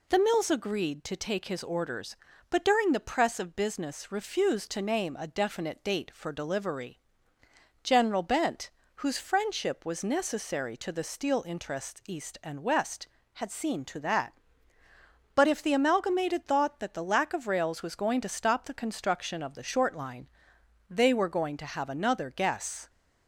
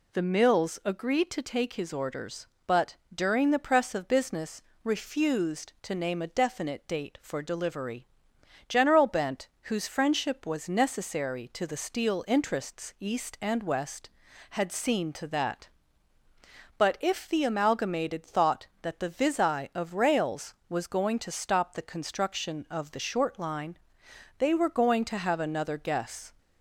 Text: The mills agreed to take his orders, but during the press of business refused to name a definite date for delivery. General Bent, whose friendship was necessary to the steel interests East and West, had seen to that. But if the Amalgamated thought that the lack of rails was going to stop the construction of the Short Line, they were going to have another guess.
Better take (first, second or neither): first